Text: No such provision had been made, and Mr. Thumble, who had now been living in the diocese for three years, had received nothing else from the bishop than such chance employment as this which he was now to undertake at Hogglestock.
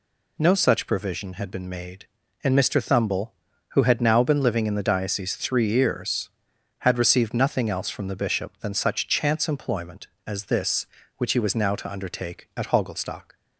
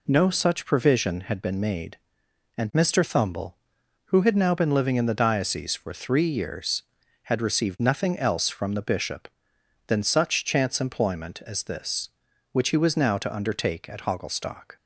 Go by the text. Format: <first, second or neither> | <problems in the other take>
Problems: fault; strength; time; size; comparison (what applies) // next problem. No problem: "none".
second | skips "for"; at 5.3 s